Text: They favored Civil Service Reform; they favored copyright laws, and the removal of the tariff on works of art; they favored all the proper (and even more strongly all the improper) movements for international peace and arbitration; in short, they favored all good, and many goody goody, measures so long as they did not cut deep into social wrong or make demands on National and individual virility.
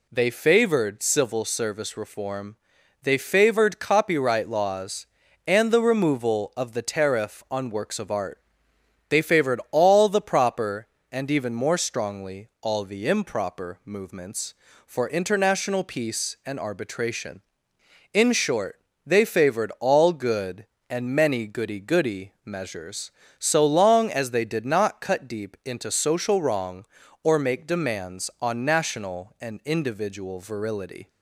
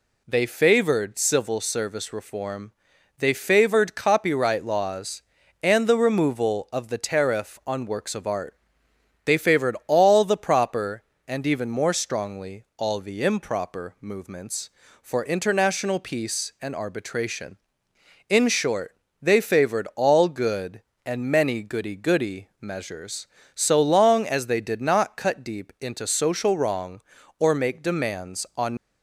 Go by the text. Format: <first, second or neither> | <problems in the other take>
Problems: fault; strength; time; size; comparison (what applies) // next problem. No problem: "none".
first | stops before "National and individual virility"; at 28.7 s